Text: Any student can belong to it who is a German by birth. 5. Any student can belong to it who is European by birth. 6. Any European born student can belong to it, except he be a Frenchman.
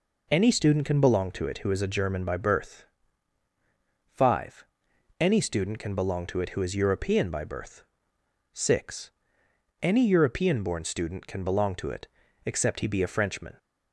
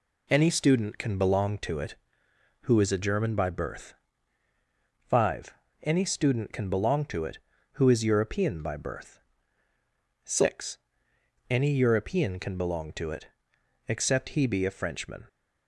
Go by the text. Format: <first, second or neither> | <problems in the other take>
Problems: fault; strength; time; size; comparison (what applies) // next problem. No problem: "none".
first | skips "born student"; at 12.3 s